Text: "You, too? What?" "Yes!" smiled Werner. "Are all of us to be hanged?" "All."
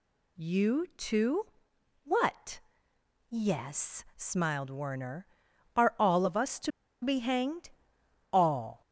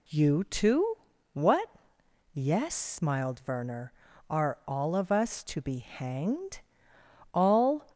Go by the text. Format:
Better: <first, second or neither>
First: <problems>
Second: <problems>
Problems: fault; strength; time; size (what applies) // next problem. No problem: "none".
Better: second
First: pauses between "to" and "be"; slight; at 6.7 s; 0.32 s long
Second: none